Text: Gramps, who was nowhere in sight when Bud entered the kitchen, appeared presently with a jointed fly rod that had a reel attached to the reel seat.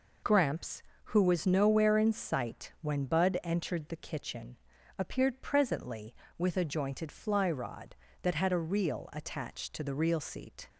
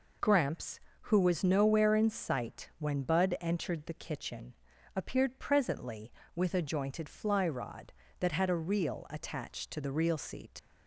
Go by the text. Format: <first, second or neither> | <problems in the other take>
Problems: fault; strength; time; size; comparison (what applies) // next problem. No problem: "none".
first | leaves "seat" unfinished; at 10.5 s; 65 ms